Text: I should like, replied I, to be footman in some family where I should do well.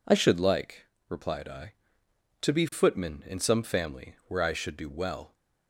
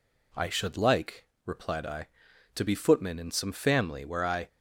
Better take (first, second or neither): first